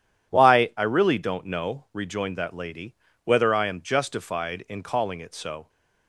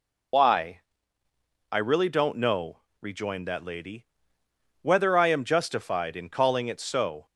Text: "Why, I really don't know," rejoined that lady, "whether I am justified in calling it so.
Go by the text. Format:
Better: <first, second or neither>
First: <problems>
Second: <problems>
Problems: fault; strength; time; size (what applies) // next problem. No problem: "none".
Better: first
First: none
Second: loses the start of "Why"; at 0.3 s; 50 ms